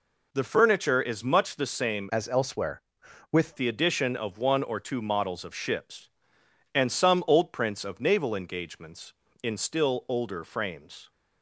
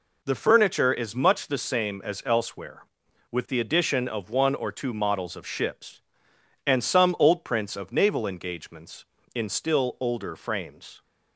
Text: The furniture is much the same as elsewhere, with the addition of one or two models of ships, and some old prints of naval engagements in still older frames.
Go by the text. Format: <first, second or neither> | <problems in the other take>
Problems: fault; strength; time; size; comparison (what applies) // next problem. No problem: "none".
second | changes voice from "as" to "with"; from 2.0 to 3.5 s; 1.5 s long